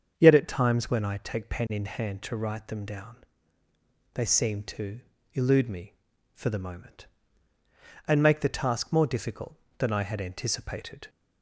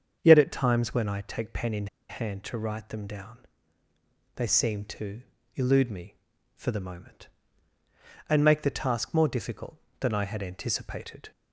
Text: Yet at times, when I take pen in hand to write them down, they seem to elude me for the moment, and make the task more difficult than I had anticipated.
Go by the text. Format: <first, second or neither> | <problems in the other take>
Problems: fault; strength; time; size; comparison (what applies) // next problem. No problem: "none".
first | starts louder than the rest; strong; until 1.2 s; 7 dB; strong in the first // pauses between "in" and "hand"; slight; at 1.8 s; 0.22 s long // pauses between "to" and "elude"; slight; at 5.2 s; 0.34 s long; slight in the first